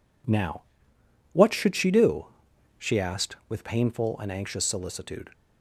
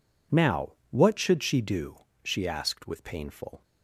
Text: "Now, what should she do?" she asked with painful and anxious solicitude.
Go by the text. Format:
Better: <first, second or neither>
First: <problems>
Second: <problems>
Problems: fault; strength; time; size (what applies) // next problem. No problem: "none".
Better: first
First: none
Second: stops before "and anxious solicitude"; at 3.6 s